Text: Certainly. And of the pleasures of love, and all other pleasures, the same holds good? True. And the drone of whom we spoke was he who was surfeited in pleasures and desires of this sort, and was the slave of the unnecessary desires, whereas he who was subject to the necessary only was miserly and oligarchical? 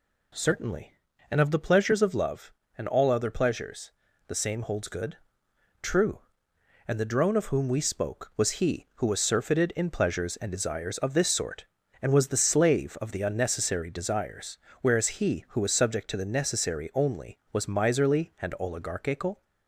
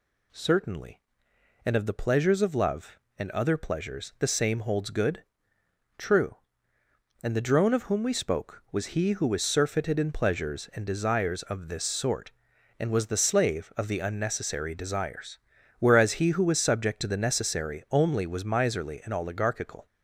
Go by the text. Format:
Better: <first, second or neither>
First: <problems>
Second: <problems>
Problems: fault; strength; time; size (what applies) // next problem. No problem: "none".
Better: first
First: none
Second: skips "all"; at 3.3 s